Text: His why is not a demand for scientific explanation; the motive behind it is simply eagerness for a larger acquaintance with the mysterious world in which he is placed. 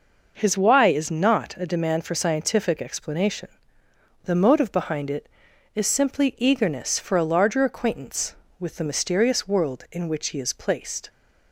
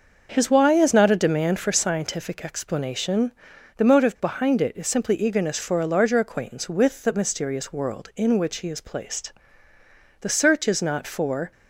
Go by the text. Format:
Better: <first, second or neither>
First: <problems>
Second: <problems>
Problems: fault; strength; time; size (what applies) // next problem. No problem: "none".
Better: first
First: none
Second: starts louder than the rest; noticeable; until 1.3 s; 6 dB // goes on to say "The search is not for"; noticeable; from 10.2 s on; 1.3 s long